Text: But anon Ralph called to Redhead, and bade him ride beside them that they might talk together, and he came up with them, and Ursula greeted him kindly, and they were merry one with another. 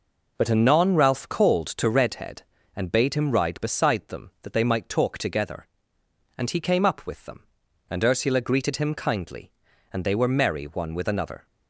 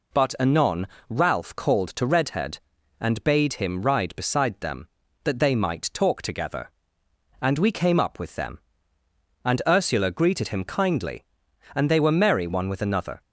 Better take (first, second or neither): first